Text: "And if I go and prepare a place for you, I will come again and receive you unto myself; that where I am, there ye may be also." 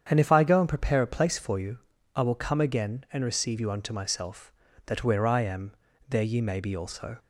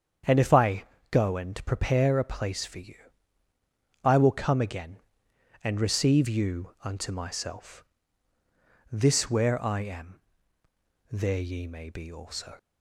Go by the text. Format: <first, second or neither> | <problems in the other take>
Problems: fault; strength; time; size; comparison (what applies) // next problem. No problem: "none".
first | starts louder than the rest; strong; until 1.5 s; 8 dB; strong in the first // pauses between "I" and "go"; slight; at 0.8 s; 0.26 s long // says "this" for "that"; at 8.9 s